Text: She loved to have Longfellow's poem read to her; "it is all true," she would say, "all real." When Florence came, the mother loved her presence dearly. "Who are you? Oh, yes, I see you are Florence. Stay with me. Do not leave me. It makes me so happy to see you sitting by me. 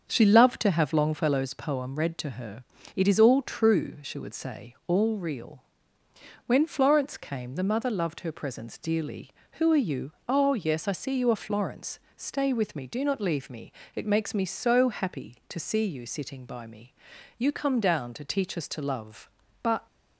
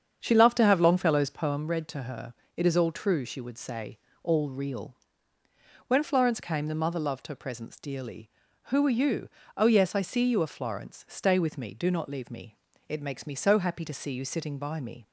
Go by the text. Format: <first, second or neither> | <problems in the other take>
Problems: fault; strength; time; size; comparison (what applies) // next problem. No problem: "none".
second | starts louder than the rest; until 1.1 s; 6.5 dB; strong in the second // goes on to say "You come down to teach us to love but"; strong; from 17.3 s on; 2.5 s long